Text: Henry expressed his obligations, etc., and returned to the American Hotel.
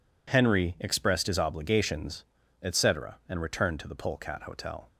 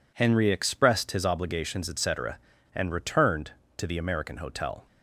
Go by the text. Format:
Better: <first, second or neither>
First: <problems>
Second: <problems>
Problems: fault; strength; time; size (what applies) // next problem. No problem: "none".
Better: second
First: says "Polecat" for "American"; at 3.9 s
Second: none